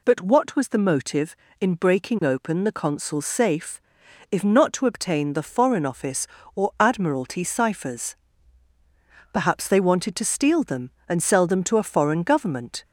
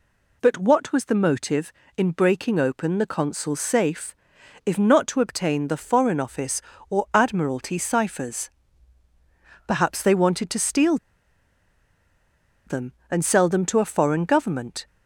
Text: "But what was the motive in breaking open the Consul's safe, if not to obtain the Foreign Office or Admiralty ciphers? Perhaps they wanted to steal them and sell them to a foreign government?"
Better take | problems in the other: first | pauses between "steal" and "them"; strong; at 10.9 s; 1.6 s long

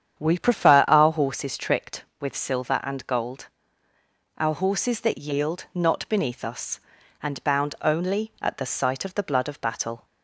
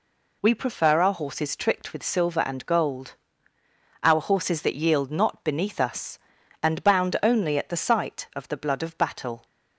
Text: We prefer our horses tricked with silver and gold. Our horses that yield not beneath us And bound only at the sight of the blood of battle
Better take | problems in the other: second | starts louder than the rest; strong; until 1.3 s; 8.5 dB

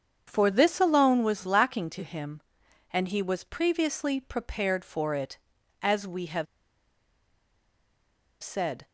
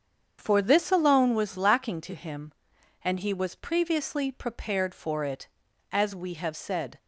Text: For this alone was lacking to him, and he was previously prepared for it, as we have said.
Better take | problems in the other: second | starts louder than the rest; strong; until 1.2 s; 7.5 dB; strong in the second // pauses between "have" and "said"; strong; at 6.4 s; 1.9 s long

